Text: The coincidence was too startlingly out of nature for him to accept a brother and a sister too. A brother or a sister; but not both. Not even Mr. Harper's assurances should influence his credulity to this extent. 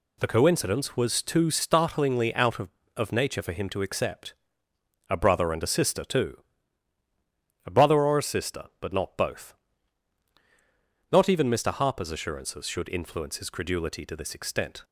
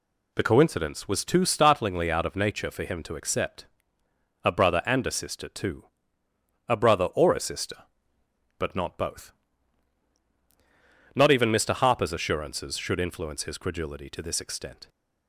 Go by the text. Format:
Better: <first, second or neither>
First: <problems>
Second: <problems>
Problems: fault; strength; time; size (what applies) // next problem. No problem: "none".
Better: second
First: says "of" twice; at 2.9 s // pauses between "accept" and "a"; noticeable; at 4.3 s; 0.76 s long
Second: pauses between "accept" and "a"; noticeable; at 3.6 s; 0.76 s long